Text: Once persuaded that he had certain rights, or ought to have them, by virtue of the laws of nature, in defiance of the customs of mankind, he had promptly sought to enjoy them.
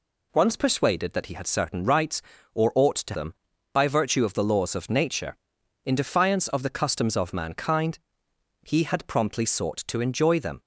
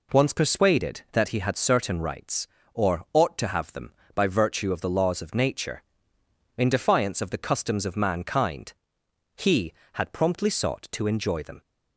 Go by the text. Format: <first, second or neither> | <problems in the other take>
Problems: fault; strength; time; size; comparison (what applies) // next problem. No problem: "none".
second | skips "have"; at 3.1 s